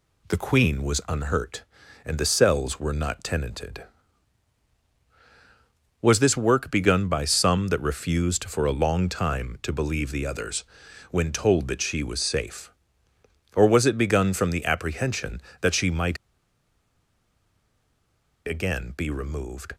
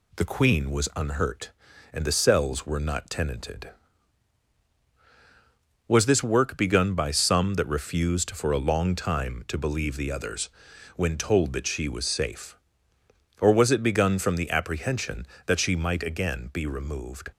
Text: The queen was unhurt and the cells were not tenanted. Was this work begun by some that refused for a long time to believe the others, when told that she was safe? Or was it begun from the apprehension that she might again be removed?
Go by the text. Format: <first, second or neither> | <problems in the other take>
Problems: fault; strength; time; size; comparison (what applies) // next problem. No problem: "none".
second | pauses between "might" and "again"; strong; at 16.1 s; 2.2 s long